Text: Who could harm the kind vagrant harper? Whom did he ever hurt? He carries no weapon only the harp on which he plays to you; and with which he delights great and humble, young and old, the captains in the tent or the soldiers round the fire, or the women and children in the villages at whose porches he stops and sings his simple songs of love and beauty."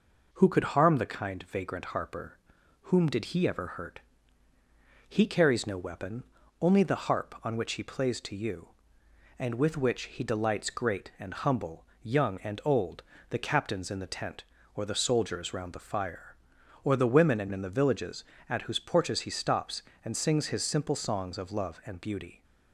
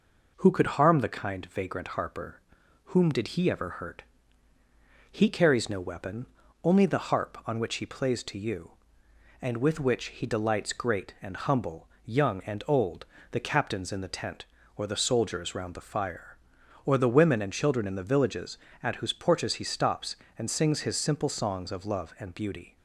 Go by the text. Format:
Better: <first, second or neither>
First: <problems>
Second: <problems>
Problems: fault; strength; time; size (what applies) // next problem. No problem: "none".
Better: second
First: pauses between "weapon" and "only"; slight; at 6.2 s; 0.36 s long // skips "children"; at 17.5 s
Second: pauses between "weapon" and "only"; slight; at 6.2 s; 0.36 s long